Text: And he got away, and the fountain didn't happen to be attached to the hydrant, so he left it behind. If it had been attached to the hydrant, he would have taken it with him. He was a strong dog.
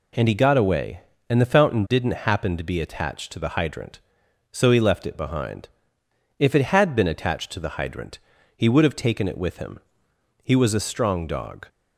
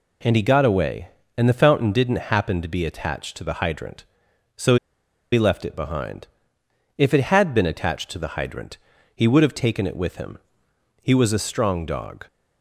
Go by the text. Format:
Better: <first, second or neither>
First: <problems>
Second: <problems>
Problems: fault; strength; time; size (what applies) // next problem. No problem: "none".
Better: first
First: none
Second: pauses between "so" and "he"; noticeable; at 4.7 s; 0.56 s long